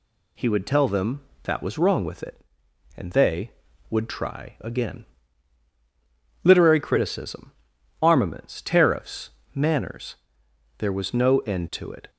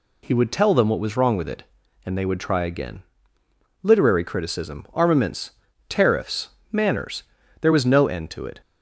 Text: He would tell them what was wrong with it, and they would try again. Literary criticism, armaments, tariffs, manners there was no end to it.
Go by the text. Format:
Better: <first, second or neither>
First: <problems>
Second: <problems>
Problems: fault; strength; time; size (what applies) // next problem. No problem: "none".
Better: second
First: says "that" for "what"; at 1.4 s // pauses between "manners" and "there"; noticeable; at 10.1 s; 0.64 s long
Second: pauses between "manners" and "there"; slight; at 7.2 s; 0.36 s long